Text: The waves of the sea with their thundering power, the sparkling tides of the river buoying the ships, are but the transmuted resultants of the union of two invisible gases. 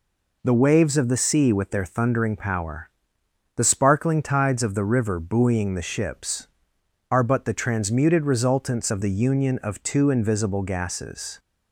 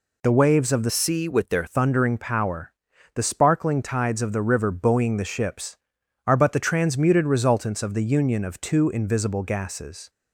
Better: first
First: none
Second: changes voice from "sea" to "their"; from 0.8 to 1.6 s; 0.8 s long

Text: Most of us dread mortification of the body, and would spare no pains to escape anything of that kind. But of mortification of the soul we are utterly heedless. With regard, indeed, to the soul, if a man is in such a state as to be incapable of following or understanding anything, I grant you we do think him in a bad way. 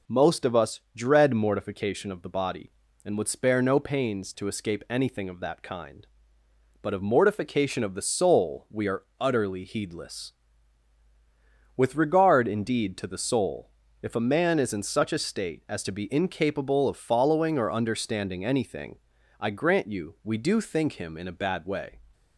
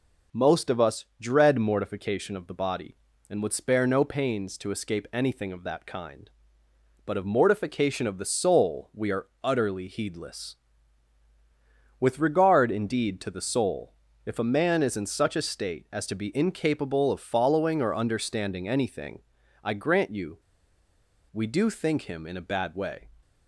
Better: first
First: pauses between "are" and "utterly"; slight; at 9.0 s; 0.16 s long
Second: pauses between "are" and "utterly"; slight; at 9.2 s; 0.16 s long // pauses between "you" and "we"; noticeable; at 20.3 s; 0.93 s long

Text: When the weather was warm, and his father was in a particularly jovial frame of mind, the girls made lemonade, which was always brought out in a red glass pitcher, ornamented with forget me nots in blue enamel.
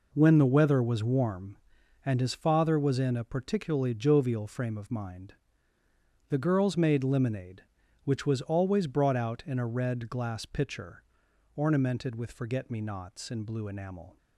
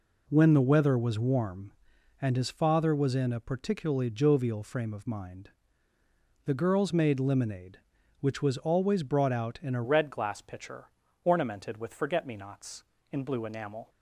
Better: first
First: none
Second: changes voice at "red"; from 9.8 s on; 4.0 s long

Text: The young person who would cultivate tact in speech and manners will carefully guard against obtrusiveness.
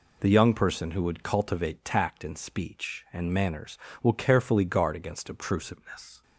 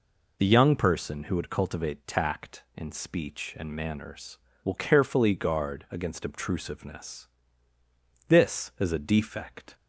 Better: first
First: none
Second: goes on to say "This is a defect"; from 8.2 s on; 1.4 s long

